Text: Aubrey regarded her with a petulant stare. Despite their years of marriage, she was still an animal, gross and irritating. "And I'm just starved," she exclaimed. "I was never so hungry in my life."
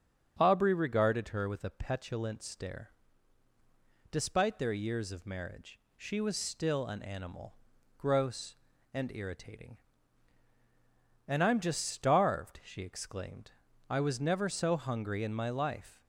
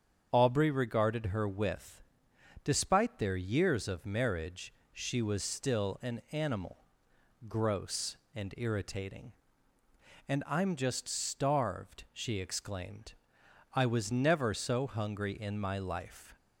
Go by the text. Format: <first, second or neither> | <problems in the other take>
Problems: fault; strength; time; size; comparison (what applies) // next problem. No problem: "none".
first | starts louder than the rest; strong; until 1.3 s; 7.5 dB; also in the first // skips "a petulant stare"; at 2.3 s